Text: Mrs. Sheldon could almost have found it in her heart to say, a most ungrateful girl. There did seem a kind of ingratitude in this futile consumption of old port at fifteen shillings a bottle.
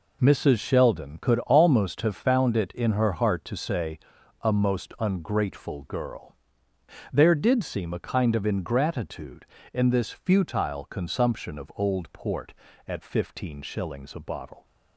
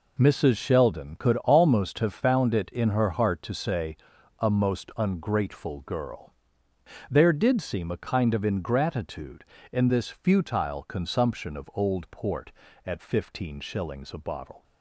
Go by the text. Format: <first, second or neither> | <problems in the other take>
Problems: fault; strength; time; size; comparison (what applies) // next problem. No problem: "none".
neither | none